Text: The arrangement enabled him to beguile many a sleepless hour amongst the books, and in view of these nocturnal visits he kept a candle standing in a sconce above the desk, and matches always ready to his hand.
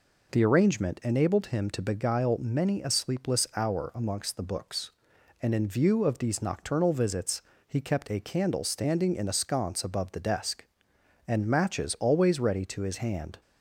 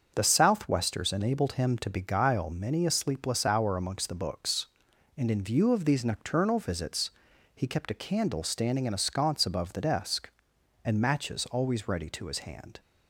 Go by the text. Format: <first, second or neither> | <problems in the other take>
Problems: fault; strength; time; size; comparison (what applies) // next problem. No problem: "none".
first | starts louder than the rest; until 1.1 s; 6.5 dB // says "southwesters" for "arrangement"; at 0.2 s // pauses between "visits" and "he"; noticeable; at 7.0 s; 0.46 s long; slight in the first